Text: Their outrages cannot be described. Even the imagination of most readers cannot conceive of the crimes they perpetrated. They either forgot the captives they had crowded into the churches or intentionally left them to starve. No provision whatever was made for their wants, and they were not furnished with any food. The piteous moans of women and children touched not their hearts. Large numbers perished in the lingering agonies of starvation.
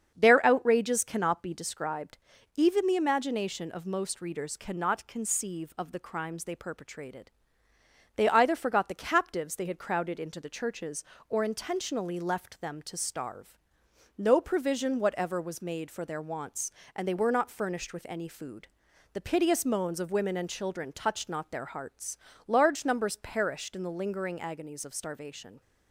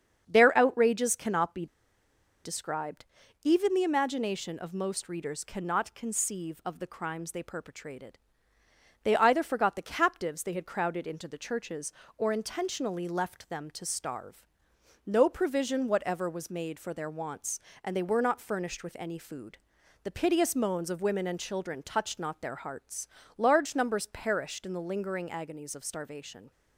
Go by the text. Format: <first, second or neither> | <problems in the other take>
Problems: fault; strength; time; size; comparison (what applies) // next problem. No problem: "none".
first | starts louder than the rest; strong; until 1.2 s; 7 dB; strong in the first // pauses between "be" and "described"; noticeable; at 1.6 s; 0.78 s long